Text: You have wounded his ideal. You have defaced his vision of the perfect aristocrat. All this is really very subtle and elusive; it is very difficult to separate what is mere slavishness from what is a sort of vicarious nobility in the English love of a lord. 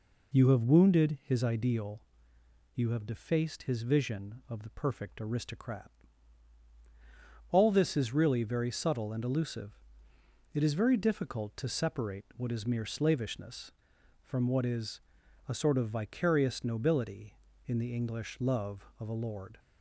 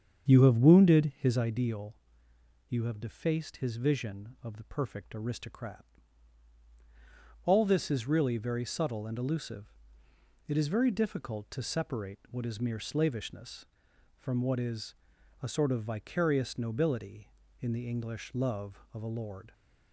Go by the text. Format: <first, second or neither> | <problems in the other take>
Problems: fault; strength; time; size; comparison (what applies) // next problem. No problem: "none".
first | starts louder than the rest; strong; until 1.5 s; 7.5 dB // pauses between "is" and "a"; noticeable; at 14.9 s; 0.46 s long; noticeable in the first